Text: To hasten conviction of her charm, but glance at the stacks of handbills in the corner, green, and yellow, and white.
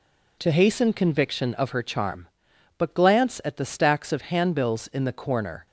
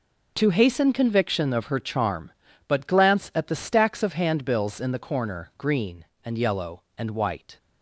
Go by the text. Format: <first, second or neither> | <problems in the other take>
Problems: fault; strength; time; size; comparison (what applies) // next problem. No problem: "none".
second | stops before "green and yellow and white"; at 5.6 s